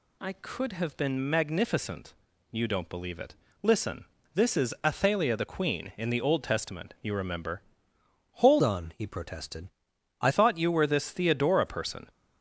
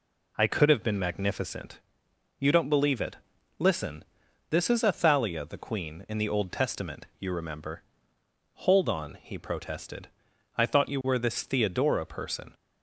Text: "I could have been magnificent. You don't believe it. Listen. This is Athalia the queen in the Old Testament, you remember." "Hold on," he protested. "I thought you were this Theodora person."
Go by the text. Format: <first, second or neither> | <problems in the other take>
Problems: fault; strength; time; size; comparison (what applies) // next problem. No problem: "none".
second | changes voice from "on" to "I"; from 8.6 to 10.2 s; 1.6 s long